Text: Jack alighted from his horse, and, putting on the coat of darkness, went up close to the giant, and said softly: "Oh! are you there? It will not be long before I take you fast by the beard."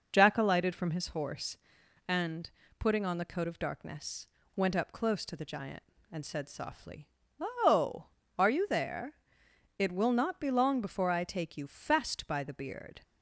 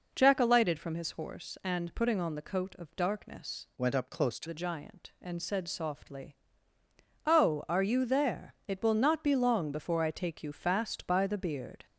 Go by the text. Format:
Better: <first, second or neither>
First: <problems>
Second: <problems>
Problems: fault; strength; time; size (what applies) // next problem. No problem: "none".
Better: first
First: none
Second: changes voice from "went" to "to"; from 3.7 to 4.4 s; 0.7 s long